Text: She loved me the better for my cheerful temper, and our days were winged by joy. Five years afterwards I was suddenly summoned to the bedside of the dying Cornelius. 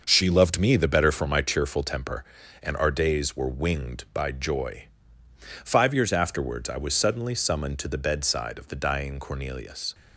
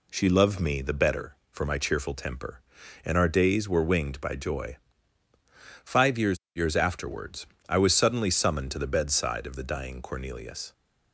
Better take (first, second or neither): first